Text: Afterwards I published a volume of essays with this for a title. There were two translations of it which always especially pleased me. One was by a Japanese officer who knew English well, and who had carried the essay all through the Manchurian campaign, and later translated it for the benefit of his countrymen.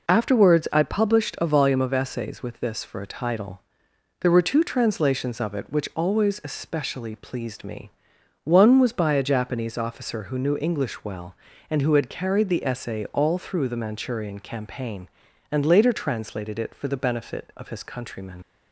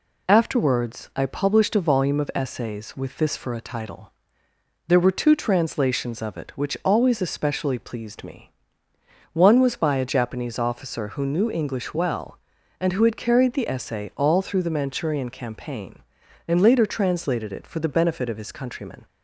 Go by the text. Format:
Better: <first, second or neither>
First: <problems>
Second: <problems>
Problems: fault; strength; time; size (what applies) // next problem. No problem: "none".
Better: second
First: leaves "countrymen" unfinished; at 18.4 s; 60 ms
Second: none